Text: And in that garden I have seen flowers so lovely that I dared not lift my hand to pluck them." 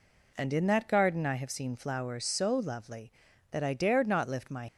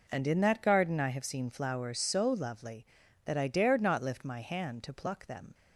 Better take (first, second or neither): second